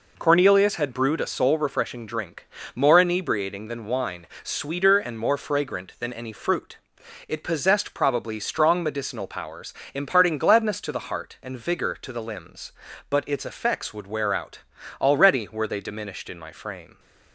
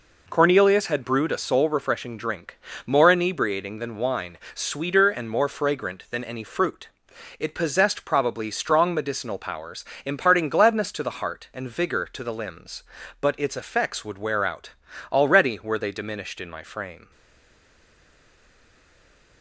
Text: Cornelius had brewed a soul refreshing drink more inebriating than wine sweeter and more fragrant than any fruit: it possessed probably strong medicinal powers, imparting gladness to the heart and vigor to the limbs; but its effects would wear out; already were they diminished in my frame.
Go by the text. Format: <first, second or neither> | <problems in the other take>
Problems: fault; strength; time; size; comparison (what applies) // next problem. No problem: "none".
first | pauses between "drink" and "more"; slight; at 2.5 s; 0.26 s long; slight in the first // pauses between "wine" and "sweeter"; slight; at 4.3 s; 0.18 s long; slight in the first // stays silent after the last word; from 17.1 s on; 2.3 s long